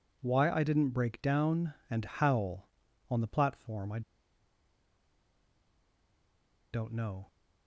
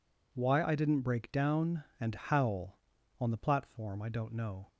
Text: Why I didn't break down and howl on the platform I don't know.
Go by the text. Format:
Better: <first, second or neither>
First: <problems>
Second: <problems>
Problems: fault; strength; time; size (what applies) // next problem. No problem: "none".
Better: second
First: pauses between "I" and "don't"; strong; at 4.0 s; 2.7 s long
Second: none